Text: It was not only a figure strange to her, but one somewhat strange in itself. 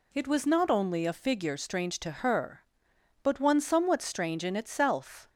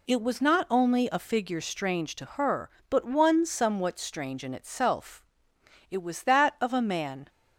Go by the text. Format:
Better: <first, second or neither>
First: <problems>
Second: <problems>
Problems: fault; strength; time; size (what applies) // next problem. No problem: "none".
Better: first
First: none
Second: goes on to say "It was that of a man"; from 5.9 s on; 1.3 s long